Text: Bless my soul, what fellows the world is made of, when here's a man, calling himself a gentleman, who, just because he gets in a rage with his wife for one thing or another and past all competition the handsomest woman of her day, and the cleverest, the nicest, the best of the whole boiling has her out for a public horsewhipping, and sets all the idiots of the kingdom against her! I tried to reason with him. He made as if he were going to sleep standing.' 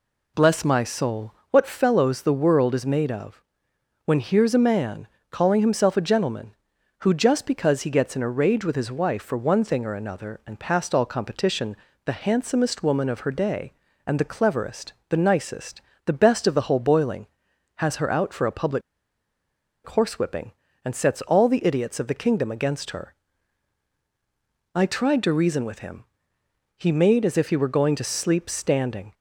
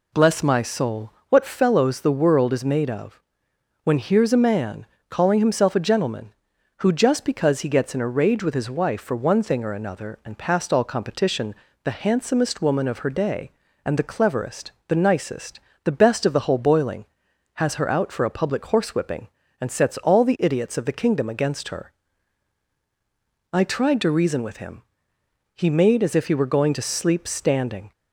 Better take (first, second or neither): second